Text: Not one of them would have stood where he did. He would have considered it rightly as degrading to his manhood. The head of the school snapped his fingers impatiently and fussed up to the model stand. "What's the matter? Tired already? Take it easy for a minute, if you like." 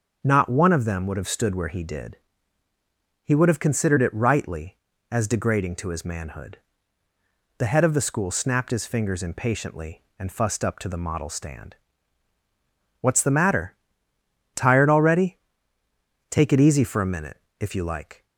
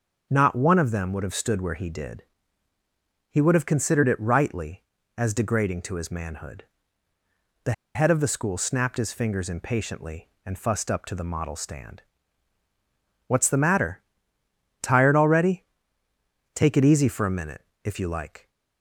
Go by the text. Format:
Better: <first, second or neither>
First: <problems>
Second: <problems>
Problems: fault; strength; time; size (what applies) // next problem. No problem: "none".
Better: first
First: starts louder than the rest; until 1.2 s; 7 dB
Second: starts louder than the rest; until 1.3 s; 7 dB // pauses between "The" and "head"; slight; at 7.7 s; 0.22 s long